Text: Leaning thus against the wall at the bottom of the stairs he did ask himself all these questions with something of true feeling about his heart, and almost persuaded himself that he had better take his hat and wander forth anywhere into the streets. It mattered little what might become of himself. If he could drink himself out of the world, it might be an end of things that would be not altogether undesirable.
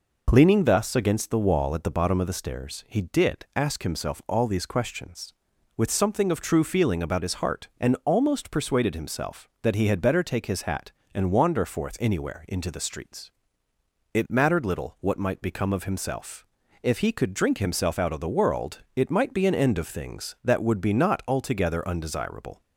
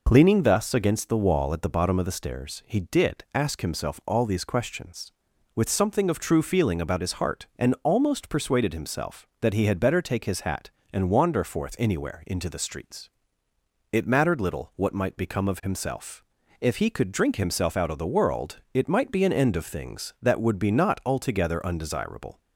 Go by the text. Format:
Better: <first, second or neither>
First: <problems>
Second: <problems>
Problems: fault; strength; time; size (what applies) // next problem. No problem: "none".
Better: neither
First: none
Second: none